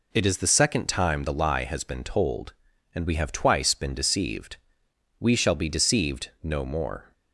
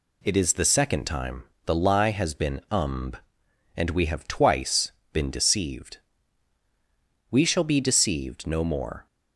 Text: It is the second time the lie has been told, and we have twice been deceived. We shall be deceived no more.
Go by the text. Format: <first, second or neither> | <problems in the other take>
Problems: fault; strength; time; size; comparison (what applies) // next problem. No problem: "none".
first | pauses between "time" and "the"; slight; at 1.4 s; 0.24 s long // says "umb" for "told"; at 2.7 s // pauses between "twice" and "been"; slight; at 4.9 s; 0.20 s long